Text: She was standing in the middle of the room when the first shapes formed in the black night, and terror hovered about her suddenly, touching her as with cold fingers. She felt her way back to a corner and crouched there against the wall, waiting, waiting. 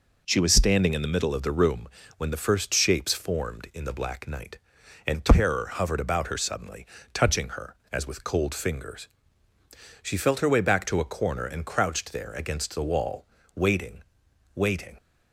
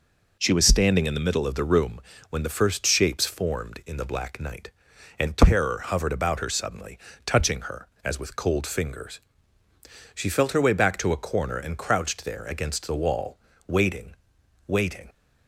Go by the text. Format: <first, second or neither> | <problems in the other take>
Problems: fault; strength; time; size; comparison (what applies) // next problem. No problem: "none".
neither | pauses between "room" and "when"; slight; the same in both